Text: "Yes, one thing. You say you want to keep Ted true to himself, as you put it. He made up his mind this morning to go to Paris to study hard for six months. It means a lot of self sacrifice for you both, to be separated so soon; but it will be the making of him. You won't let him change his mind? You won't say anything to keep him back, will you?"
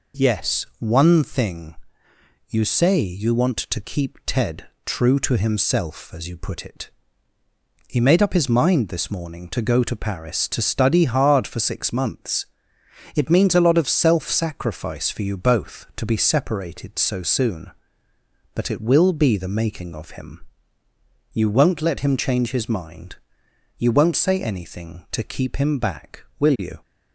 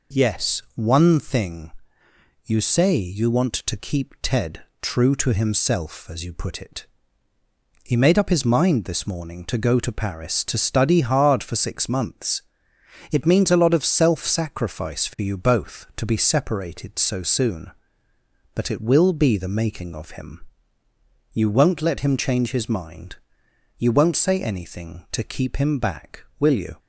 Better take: neither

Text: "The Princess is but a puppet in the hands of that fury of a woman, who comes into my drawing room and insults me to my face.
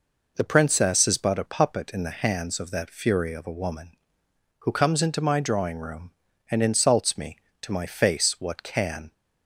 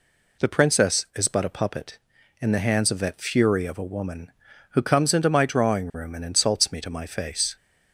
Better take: second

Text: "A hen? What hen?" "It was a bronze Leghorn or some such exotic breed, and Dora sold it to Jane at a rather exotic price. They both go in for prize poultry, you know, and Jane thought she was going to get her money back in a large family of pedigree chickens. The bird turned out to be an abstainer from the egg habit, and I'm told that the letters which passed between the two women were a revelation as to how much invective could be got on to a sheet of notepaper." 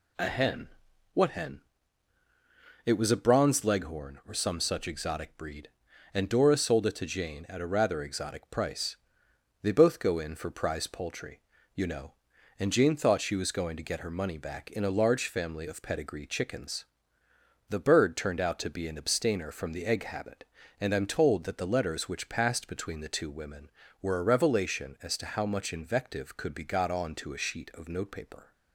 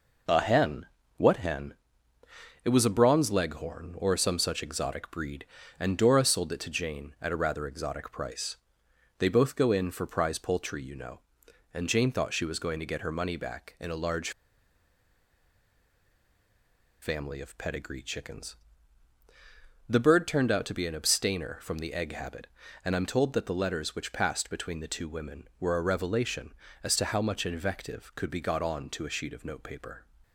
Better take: first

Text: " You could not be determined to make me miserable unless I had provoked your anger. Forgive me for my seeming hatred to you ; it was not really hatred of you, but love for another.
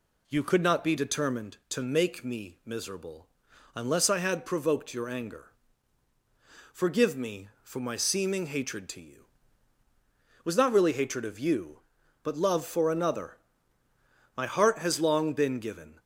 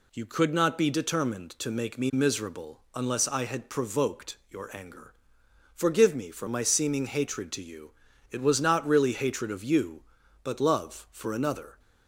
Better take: second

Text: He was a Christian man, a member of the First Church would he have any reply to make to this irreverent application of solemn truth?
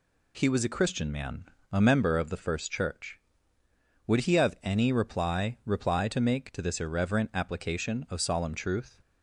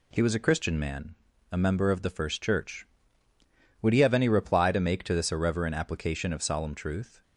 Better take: second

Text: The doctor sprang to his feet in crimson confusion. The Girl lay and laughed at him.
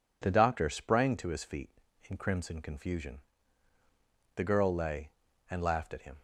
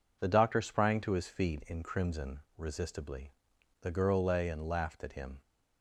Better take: first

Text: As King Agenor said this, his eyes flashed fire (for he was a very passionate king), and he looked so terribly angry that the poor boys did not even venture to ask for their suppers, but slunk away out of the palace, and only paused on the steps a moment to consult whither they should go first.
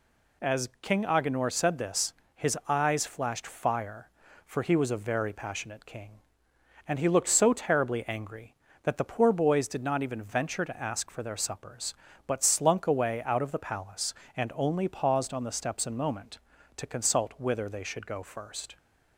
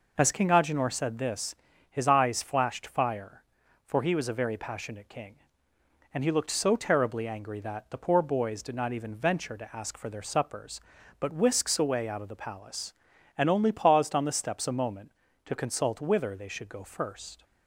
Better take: first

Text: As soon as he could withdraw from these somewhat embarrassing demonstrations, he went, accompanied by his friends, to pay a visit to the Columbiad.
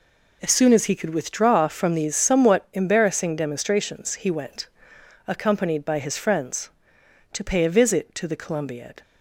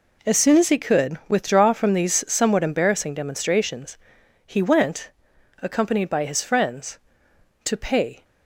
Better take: first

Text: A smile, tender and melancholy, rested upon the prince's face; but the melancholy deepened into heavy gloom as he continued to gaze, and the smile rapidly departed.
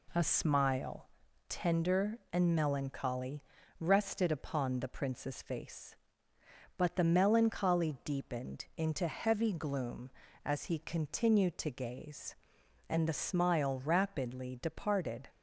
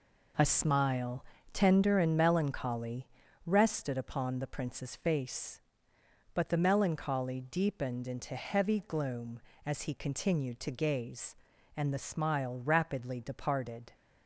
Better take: neither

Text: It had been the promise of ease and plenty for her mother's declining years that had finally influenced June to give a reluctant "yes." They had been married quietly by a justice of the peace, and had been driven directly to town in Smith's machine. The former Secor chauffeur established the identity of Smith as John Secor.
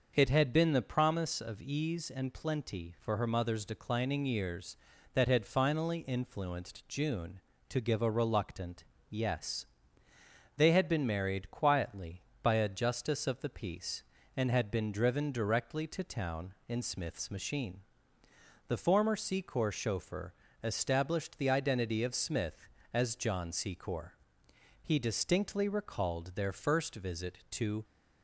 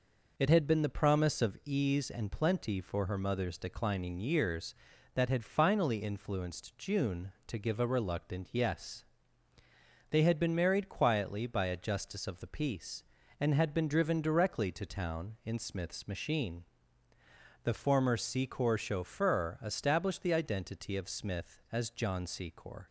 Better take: second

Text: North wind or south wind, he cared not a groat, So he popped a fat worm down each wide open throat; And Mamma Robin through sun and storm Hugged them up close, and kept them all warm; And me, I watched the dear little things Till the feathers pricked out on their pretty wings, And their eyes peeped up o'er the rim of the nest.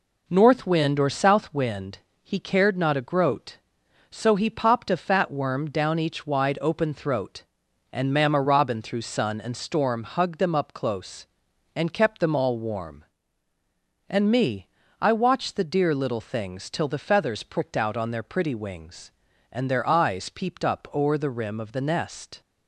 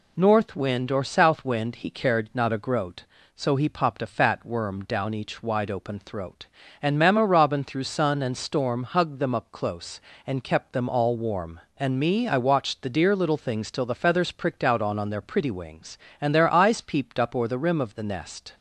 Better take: first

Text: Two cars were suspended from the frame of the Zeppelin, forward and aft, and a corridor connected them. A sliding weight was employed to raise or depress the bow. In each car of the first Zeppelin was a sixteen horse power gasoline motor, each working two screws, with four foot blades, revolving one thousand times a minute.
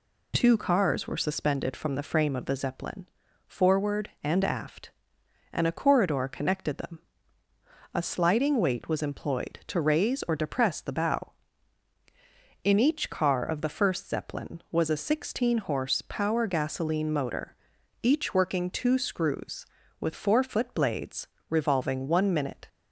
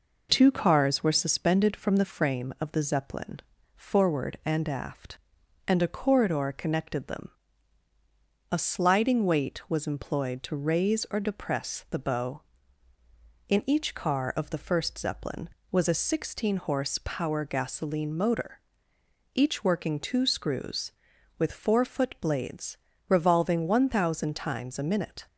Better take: second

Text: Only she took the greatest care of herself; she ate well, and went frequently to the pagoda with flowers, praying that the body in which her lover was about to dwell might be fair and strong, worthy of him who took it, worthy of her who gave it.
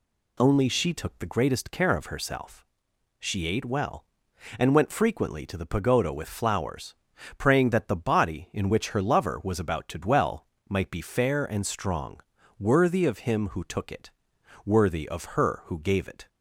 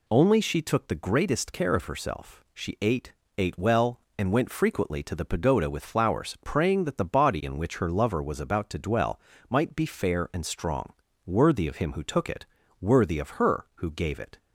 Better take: first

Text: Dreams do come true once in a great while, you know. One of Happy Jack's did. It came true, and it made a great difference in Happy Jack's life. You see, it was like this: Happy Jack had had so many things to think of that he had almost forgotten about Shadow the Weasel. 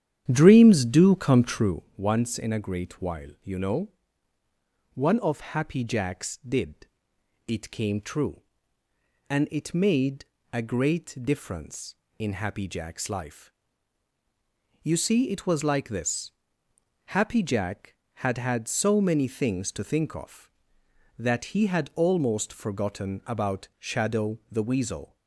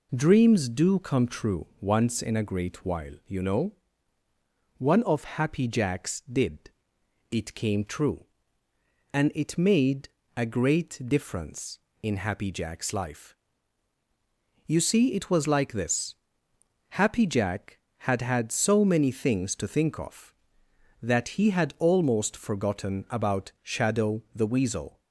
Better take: second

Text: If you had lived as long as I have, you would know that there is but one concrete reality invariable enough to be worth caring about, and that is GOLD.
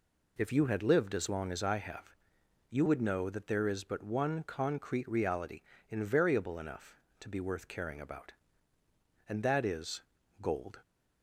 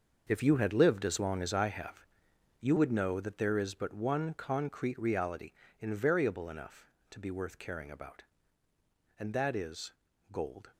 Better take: first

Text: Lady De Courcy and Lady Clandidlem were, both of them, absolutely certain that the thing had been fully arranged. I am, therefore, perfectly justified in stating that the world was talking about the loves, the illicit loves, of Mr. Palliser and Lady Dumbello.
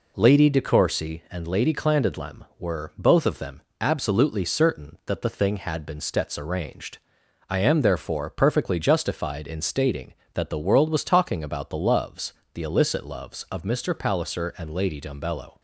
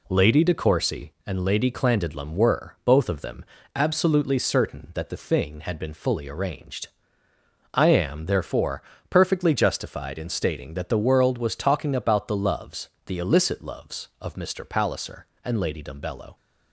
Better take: second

